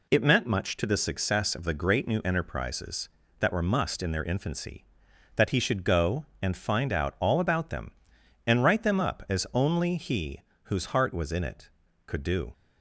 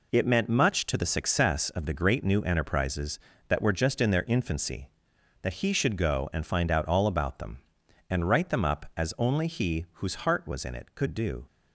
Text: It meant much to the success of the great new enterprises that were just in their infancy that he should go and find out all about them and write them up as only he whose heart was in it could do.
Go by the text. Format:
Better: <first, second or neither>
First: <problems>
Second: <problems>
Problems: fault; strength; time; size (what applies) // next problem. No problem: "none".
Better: second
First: says "must" for "just"; at 3.6 s // pauses between "he" and "whose"; slight; at 10.4 s; 0.24 s long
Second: none